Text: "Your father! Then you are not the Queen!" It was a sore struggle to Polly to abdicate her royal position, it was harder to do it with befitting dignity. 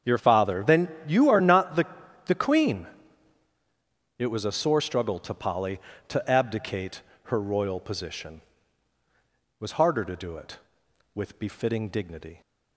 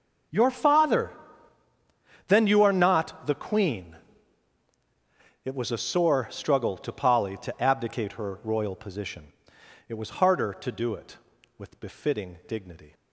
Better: second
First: starts louder than the rest; strong; until 1.2 s; 8 dB // pauses between "Then" and "you"; slight; at 0.8 s; 0.18 s long // says "the" twice; at 2.2 s // pauses between "abdicate" and "her"; slight; at 7.0 s; 0.24 s long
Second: starts louder than the rest; until 2.4 s; 6 dB

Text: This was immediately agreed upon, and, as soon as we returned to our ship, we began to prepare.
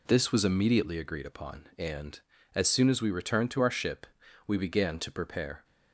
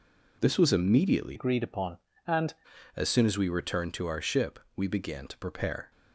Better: first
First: none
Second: changes voice from "agreed" to "and"; from 1.3 to 2.5 s; 1.2 s long

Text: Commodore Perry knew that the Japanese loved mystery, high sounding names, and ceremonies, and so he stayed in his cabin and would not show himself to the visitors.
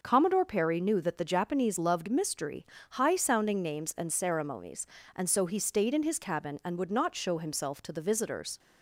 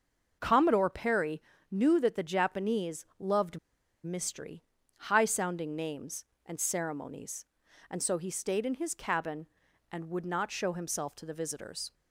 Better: first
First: none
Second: starts louder than the rest; until 1.4 s; 6 dB // pauses between "Perry" and "knew"; slight; at 1.4 s; 0.28 s long // pauses between "loved" and "mystery"; at 3.5 s; 0.45 s long

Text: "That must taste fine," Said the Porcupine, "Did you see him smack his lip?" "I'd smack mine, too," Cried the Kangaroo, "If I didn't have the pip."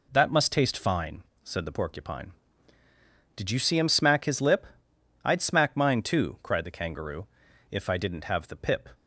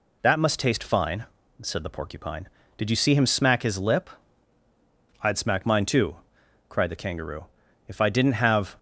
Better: first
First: none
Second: stops before "the pip"; at 8.7 s

